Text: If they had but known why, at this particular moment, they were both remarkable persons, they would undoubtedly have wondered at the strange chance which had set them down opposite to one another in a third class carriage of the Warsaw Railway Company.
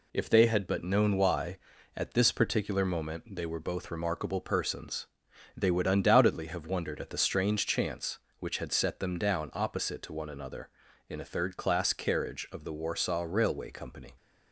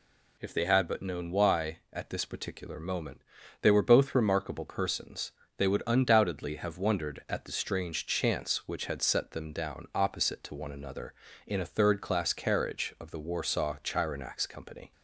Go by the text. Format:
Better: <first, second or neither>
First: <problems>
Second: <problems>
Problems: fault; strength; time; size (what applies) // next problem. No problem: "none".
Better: first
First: none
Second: says "Chironax" for "Railway"; at 13.8 s